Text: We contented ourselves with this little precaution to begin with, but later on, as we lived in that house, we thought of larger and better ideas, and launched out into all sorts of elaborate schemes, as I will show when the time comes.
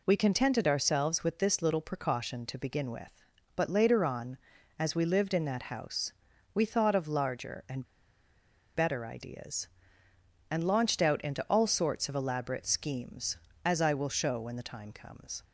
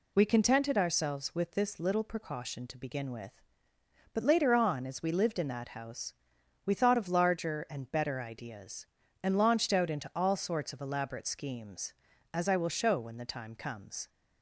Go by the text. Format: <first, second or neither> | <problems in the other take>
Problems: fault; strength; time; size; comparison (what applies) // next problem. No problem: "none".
second | pauses between "and" and "better"; noticeable; at 7.8 s; 0.90 s long